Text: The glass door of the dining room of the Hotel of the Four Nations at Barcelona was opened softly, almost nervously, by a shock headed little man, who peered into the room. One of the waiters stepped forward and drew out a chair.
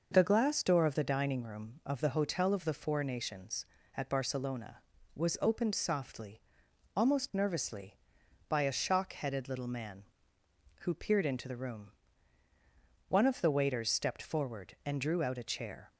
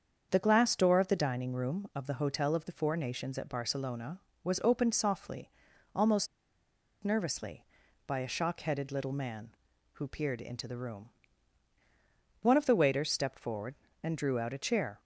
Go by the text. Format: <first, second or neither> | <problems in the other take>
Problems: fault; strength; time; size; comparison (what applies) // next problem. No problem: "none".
first | starts louder than the rest; strong; until 1.3 s; 7 dB // pauses between "almost" and "nervously"; noticeable; at 6.2 s; 0.76 s long